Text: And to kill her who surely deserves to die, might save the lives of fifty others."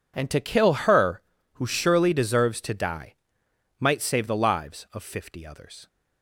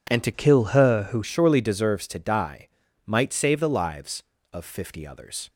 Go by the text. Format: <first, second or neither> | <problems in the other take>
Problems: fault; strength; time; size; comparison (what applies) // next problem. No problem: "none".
first | changes voice from "kill" to "who"; from 0.3 to 1.2 s; 0.9 s long